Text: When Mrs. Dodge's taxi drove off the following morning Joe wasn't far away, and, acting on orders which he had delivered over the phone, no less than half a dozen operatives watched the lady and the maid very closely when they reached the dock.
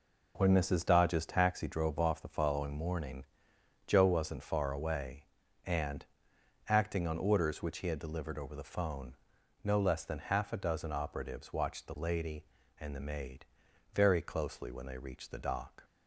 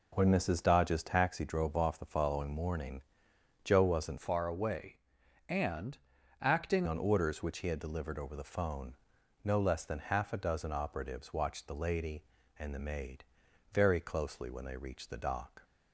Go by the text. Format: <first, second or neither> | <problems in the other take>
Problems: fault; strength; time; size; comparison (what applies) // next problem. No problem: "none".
first | pauses between "morning" and "Joe"; noticeable; at 3.0 s; 0.62 s long; noticeable in the first // changes voice from "far" to "acting"; from 4.1 to 6.8 s; 2.7 s long // pauses between "maid" and "very"; noticeable; at 13.2 s; 0.50 s long; noticeable in the first